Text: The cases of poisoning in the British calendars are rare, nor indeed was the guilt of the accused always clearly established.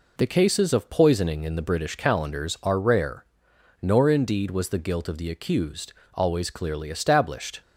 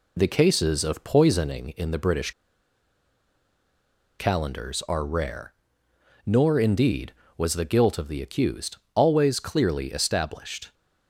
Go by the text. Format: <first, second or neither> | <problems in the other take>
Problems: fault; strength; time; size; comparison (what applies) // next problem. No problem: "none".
first | pauses between "British" and "calendars"; strong; at 2.3 s; 1.8 s long // pauses between "accused" and "always"; slight; at 8.7 s; 0.18 s long; slight in the first